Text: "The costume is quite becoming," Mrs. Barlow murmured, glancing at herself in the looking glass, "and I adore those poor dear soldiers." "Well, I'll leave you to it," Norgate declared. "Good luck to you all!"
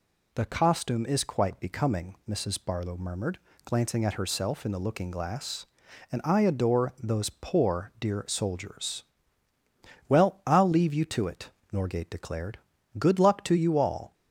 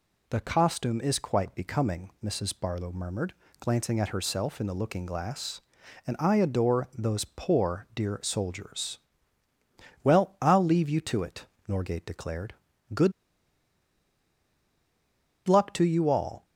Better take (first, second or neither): first